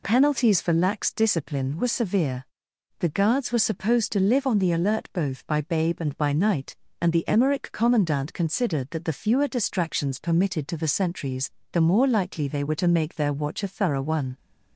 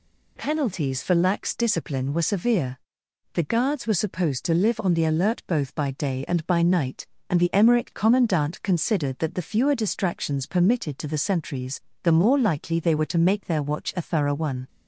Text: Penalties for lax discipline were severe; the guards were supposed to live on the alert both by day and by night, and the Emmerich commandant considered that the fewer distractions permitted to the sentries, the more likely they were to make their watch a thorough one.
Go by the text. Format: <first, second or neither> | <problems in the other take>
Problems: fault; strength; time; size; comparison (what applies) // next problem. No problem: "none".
second | says "babe" for "day"; at 5.6 s